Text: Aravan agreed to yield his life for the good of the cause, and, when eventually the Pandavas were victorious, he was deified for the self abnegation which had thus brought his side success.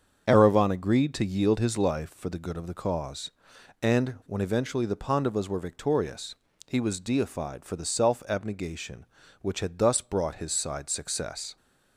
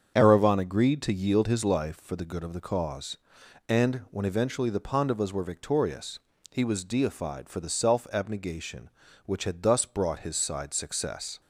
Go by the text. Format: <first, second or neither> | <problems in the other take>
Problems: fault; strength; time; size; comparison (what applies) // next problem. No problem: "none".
neither | starts louder than the rest; strong; the same in both